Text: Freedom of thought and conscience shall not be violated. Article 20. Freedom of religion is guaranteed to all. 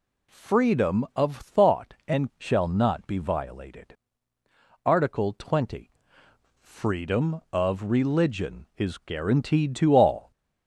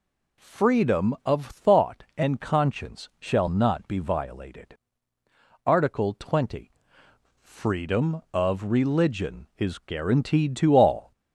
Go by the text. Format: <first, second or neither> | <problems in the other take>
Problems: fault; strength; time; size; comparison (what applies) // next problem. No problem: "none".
second | skips "conscience"; at 2.3 s